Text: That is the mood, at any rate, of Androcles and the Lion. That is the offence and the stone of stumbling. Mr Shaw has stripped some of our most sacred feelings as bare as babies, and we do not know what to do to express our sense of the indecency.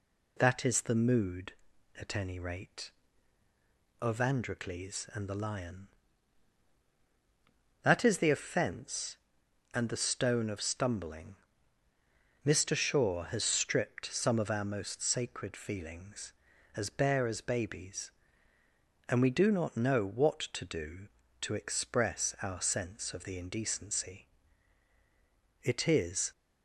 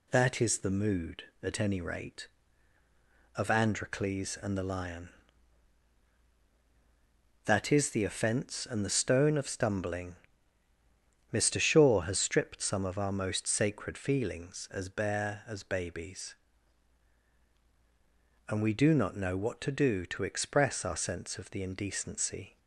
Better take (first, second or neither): second